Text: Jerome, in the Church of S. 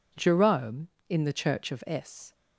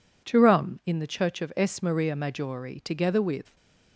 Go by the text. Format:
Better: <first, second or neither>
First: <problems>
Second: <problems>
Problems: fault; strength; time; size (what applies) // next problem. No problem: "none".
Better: first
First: none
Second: goes on to say "Maria Maggiore together with"; strong; from 1.8 s on; 1.7 s long